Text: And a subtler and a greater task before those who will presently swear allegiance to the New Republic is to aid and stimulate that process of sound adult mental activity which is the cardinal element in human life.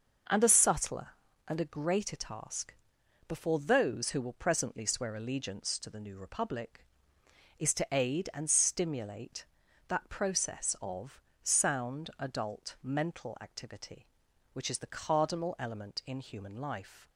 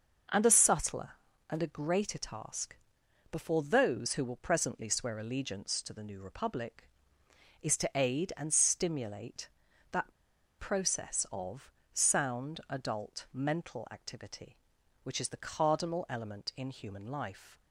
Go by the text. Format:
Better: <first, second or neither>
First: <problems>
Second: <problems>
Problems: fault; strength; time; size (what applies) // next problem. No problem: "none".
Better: first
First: starts louder than the rest; noticeable; until 1.6 s; 6 dB // pauses between "task" and "before"; noticeable; at 2.7 s; 0.54 s long // pauses between "of" and "sound"; slight; at 11.1 s; 0.22 s long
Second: starts louder than the rest; noticeable; until 1.6 s; 6 dB // pauses between "task" and "before"; noticeable; at 2.7 s; 0.56 s long // pauses between "that" and "process"; at 10.1 s; 0.45 s long // pauses between "of" and "sound"; slight; at 11.6 s; 0.22 s long